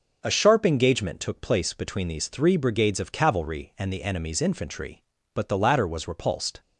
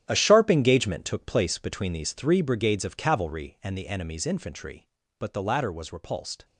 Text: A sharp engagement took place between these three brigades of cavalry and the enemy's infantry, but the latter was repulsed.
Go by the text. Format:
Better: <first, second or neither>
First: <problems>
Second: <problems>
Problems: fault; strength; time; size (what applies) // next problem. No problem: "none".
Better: first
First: none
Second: gets quieter; strong; throughout; 12.5 dB